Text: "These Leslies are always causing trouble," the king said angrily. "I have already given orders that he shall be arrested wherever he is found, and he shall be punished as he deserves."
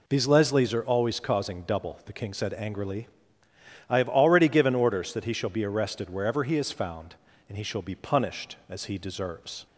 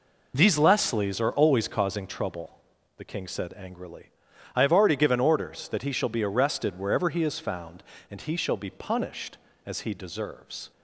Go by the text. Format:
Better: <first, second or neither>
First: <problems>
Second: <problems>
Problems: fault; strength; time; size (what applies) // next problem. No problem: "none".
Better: second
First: says "double" for "trouble"; at 1.6 s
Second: none